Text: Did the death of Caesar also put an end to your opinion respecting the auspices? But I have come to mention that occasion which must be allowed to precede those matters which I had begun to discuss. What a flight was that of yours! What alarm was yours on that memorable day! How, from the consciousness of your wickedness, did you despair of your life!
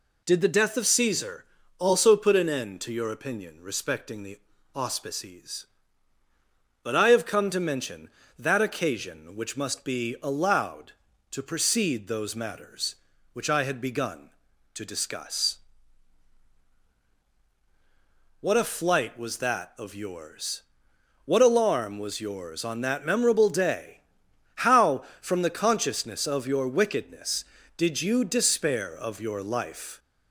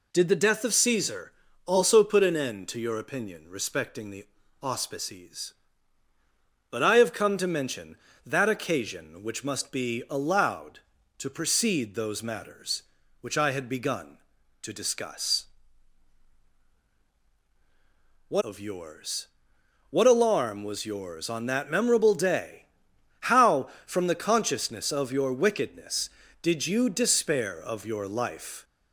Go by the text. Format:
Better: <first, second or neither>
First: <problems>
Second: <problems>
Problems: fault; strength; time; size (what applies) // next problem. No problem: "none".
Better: first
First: pauses between "Caesar" and "also"; slight; at 1.4 s; 0.36 s long // pauses between "the" and "auspices"; slight; at 4.3 s; 0.34 s long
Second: pauses between "Caesar" and "also"; slight; at 1.3 s; 0.36 s long // pauses between "the" and "auspices"; slight; at 4.2 s; 0.34 s long // skips "a flight was that"; at 18.4 s